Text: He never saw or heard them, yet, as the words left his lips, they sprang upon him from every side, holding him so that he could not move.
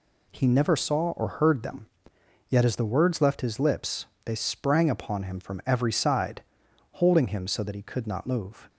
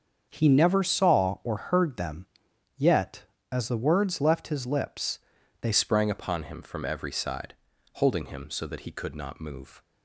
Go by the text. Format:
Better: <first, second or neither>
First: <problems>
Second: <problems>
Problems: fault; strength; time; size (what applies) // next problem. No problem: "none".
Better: first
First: none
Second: starts louder than the rest; strong; until 1.2 s; 7 dB // changes voice at "sprang"; from 5.7 s on; 4.1 s long